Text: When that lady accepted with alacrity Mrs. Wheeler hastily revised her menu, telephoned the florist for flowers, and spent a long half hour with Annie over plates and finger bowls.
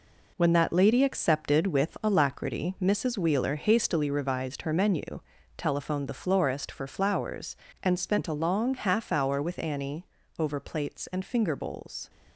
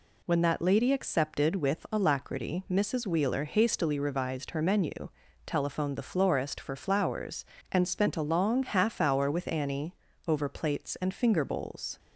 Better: second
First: gets quieter; strong; throughout; 7 dB // pauses between "Annie" and "over"; slight; at 10.0 s; 0.34 s long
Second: pauses between "Annie" and "over"; slight; at 9.9 s; 0.34 s long

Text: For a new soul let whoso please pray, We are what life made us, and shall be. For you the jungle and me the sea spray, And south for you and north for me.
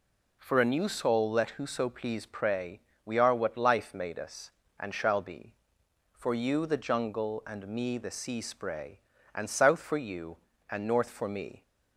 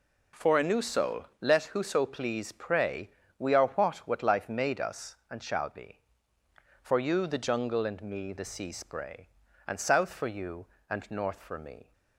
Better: first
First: none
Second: says "what" twice; at 3.9 s

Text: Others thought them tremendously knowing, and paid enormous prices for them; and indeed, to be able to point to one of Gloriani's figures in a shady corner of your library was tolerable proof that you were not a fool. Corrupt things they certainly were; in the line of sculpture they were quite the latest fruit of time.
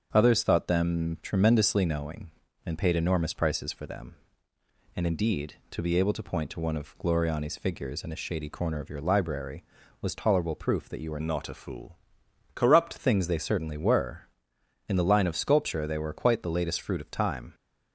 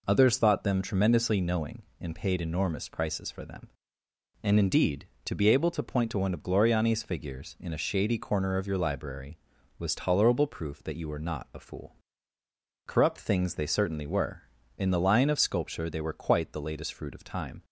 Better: second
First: starts louder than the rest; until 1.1 s; 7 dB // changes voice from "not" to "Corrupt"; from 11.2 to 12.9 s; 1.7 s long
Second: none

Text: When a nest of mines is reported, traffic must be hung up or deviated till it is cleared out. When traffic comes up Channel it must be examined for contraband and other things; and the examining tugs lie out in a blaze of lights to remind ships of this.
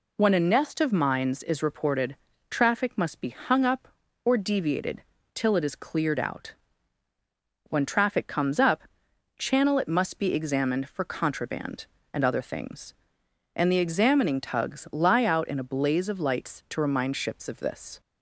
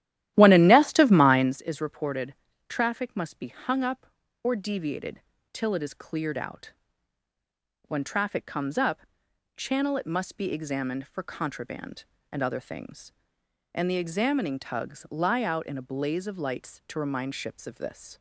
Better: first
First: pauses between "deviated" and "till"; slight; at 5.0 s; 0.32 s long // pauses between "up" and "Channel"; noticeable; at 8.8 s; 0.56 s long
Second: starts louder than the rest; strong; until 1.6 s; 13 dB // pauses between "deviated" and "till"; slight; at 5.2 s; 0.32 s long // pauses between "up" and "Channel"; noticeable; at 9.0 s; 0.56 s long

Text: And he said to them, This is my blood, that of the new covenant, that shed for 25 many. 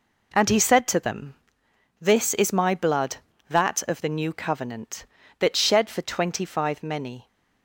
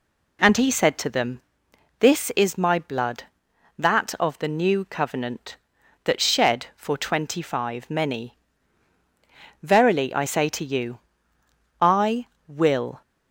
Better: first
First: none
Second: goes on to say "Verily I say to you I will"; strong; from 9.6 s on; 3.4 s long

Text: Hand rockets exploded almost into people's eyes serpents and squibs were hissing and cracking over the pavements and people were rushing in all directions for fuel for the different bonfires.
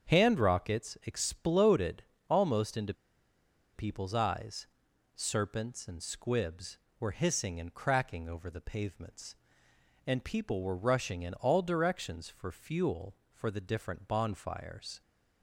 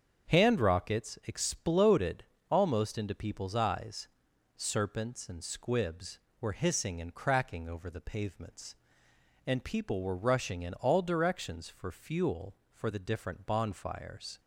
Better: second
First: starts louder than the rest; strong; until 1.1 s; 7 dB // pauses between "exploded" and "almost"; slight; at 2.0 s; 0.26 s long // pauses between "into" and "people's"; noticeable; at 2.9 s; 0.82 s long // pauses between "eyes" and "serpents"; noticeable; at 4.6 s; 0.48 s long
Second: starts louder than the rest; strong; until 1.3 s; 7 dB // pauses between "exploded" and "almost"; slight; at 2.2 s; 0.26 s long // pauses between "eyes" and "serpents"; noticeable; at 4.0 s; 0.48 s long

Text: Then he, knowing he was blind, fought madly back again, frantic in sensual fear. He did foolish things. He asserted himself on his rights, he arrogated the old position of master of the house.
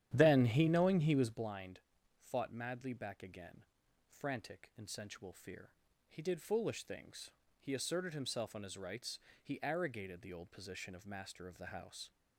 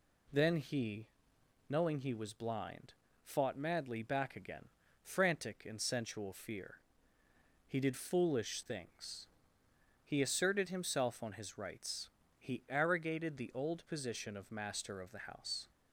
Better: second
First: starts louder than the rest; strong; until 1.5 s; 11 dB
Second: none

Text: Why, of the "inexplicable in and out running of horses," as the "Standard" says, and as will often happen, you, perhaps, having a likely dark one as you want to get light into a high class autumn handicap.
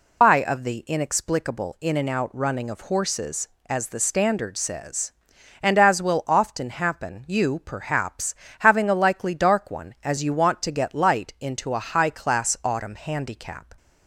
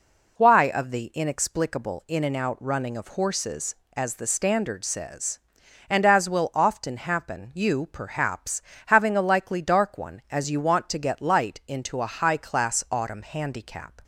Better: second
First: loses the start of "Why"; at 0.2 s; 105 ms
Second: none

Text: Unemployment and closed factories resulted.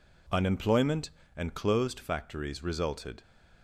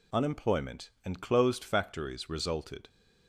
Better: neither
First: none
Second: none

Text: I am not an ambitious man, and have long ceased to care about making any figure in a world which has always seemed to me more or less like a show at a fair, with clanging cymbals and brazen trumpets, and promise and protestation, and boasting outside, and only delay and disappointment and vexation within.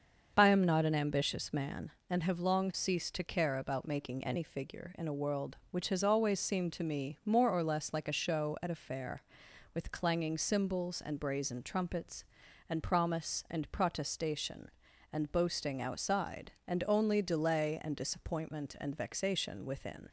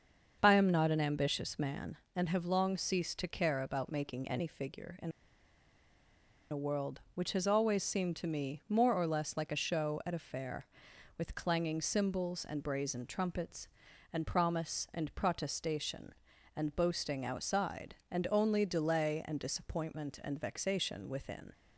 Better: first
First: starts louder than the rest; until 1.3 s; 6.5 dB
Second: starts louder than the rest; until 1.4 s; 6.5 dB // pauses between "in" and "a"; strong; at 5.1 s; 1.4 s long

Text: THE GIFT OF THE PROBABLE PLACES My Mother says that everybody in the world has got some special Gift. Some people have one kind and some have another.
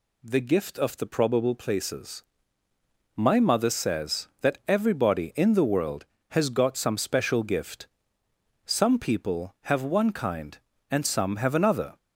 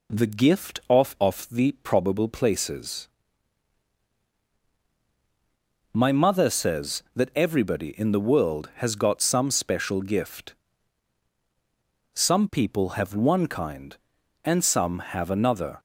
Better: first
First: pauses between "PLACES" and "My"; noticeable; at 2.2 s; 0.92 s long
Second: says "OF" twice; at 1.2 s // pauses between "PLACES" and "My"; strong; at 3.0 s; 2.8 s long

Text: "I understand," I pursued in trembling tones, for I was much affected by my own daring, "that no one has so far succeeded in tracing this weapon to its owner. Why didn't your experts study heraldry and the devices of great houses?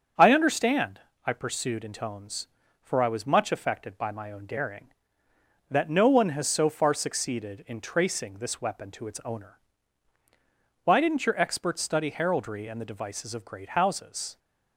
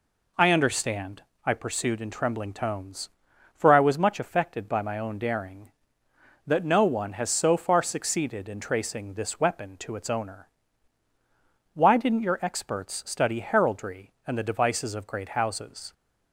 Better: second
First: starts louder than the rest; strong; until 1.4 s; 7.5 dB // skips "trembling"; at 1.9 s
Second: none

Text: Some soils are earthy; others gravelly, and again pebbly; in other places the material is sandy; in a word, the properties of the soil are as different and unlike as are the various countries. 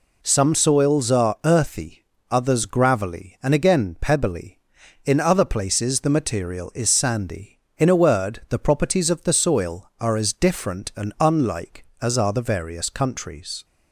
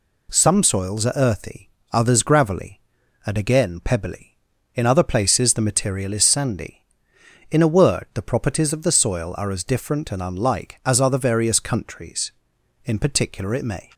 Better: first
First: none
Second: goes on to say "In particular it may"; noticeable; from 12.8 s on; 1.0 s long

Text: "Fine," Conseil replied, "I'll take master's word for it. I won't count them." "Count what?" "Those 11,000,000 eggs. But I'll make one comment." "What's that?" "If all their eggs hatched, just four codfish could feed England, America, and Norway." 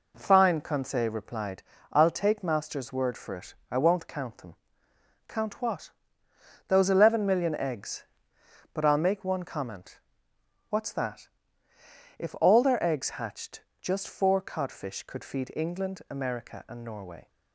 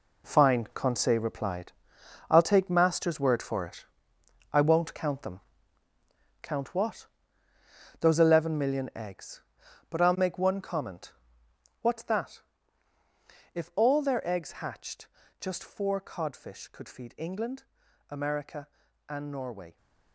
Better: first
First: none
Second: gets quieter; strong; throughout; 9.5 dB

